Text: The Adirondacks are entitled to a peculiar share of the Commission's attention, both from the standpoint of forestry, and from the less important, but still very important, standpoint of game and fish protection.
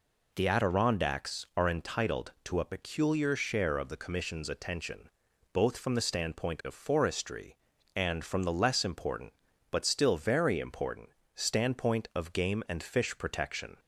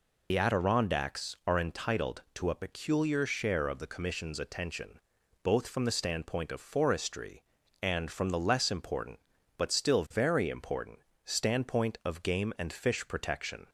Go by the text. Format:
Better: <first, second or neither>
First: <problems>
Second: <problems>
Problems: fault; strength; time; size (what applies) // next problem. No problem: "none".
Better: first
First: none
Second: loses the start of "The"; at 0.3 s; 55 ms